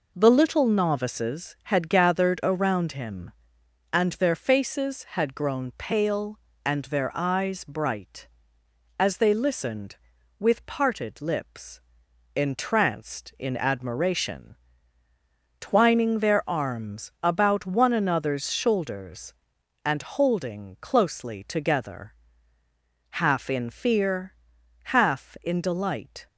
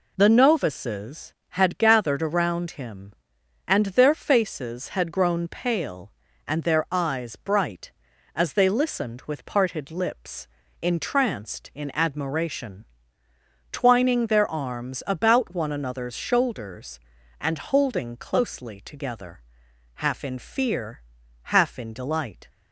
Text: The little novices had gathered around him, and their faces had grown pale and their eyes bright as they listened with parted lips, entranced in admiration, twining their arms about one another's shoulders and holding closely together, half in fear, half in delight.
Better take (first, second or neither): first